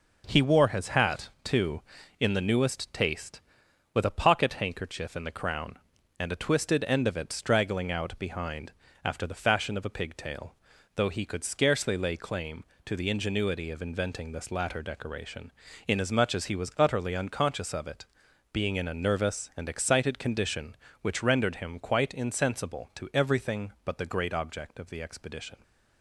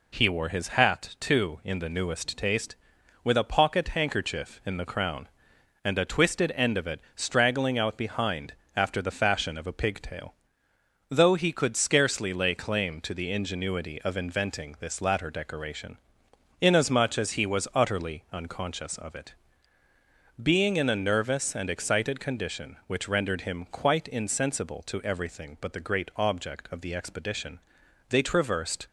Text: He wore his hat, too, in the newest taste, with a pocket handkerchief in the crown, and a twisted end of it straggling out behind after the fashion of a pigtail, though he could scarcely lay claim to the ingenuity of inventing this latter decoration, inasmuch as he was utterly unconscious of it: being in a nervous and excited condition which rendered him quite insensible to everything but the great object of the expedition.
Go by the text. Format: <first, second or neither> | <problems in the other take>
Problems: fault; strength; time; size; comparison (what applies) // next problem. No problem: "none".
first | pauses between "it" and "straggling"; slight; at 6.9 s; 0.16 s long // pauses between "behind" and "after"; slight; at 8.5 s; 0.22 s long; slight in the first // goes on to say "They traversed"; noticeable; from 28.0 s on; 0.76 s long